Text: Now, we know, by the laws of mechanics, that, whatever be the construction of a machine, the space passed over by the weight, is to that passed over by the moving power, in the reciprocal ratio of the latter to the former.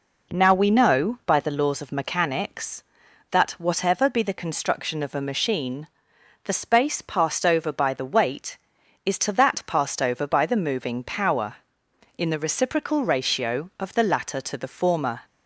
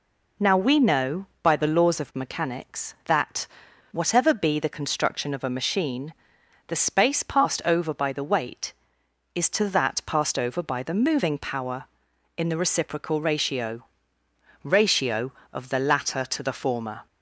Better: first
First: none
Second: says "ratio" twice; at 14.6 s

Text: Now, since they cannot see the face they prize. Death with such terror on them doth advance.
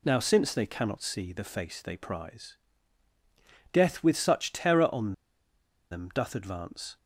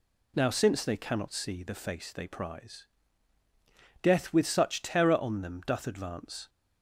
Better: second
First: pauses between "on" and "them"; noticeable; at 5.1 s; 0.79 s long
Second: none

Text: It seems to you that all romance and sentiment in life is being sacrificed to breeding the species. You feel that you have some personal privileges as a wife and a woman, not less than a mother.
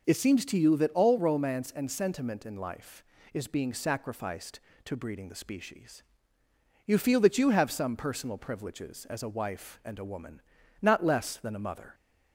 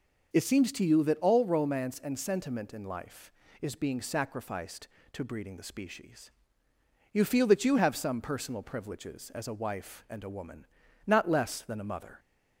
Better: neither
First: none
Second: none

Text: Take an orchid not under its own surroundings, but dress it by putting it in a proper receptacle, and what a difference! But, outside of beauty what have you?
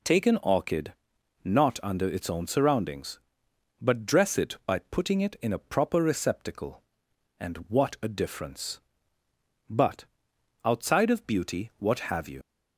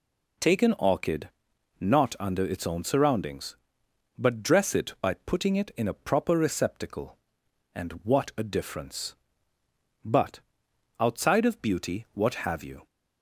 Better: second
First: pauses between "orchid" and "not"; noticeable; at 0.9 s; 0.48 s long // leaves "you" unfinished; at 12.4 s; 90 ms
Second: pauses between "orchid" and "not"; noticeable; at 1.2 s; 0.48 s long

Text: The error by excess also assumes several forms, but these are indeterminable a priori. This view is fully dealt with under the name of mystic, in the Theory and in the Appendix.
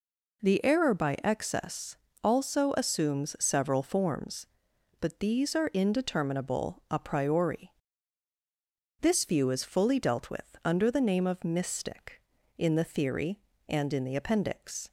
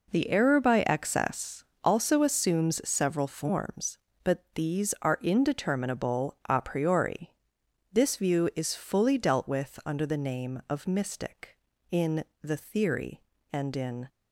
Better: first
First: pauses between "excess" and "also"; slight; at 1.9 s; 0.26 s long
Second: pauses between "excess" and "also"; slight; at 1.6 s; 0.20 s long // pauses between "in" and "the"; slight; at 12.2 s; 0.18 s long // stops before "the Appendix"; at 14.0 s

